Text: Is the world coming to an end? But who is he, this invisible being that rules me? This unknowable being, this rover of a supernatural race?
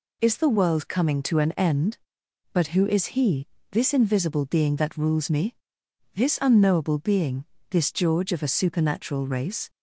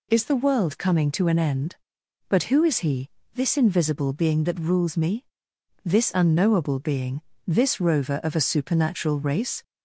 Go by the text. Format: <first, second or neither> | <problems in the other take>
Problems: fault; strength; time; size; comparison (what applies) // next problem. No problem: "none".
second | says "george" for "rover"; at 7.9 s